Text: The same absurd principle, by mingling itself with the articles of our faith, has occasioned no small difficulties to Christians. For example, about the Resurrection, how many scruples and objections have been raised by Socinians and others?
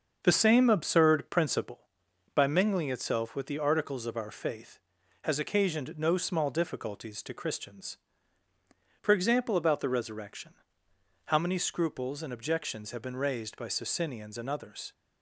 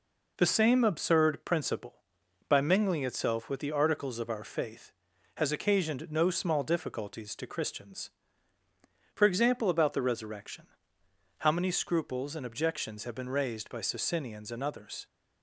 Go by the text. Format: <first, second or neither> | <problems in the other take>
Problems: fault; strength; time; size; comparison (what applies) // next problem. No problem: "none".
second | starts louder than the rest; until 1.8 s; 6.5 dB